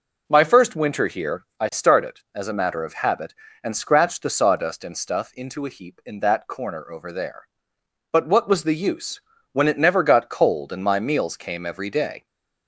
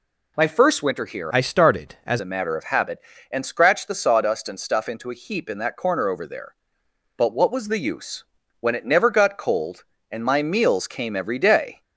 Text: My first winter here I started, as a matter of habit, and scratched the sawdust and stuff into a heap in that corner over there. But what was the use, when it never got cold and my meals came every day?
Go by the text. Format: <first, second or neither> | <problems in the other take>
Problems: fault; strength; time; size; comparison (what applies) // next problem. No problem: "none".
first | changes voice from "I" to "as"; from 1.3 to 2.1 s; 0.8 s long